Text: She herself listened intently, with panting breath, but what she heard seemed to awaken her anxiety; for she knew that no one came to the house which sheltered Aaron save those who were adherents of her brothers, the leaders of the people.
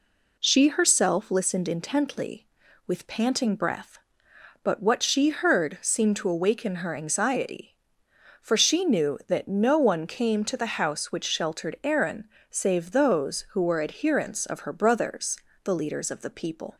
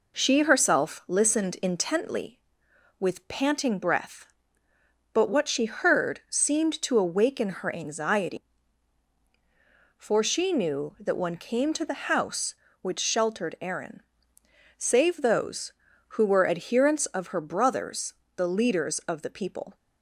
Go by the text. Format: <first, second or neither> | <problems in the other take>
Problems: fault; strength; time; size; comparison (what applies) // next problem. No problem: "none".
first | skips "no"; at 11.1 s // pauses between "Aaron" and "save"; noticeable; at 14.0 s; 0.74 s long; slight in the first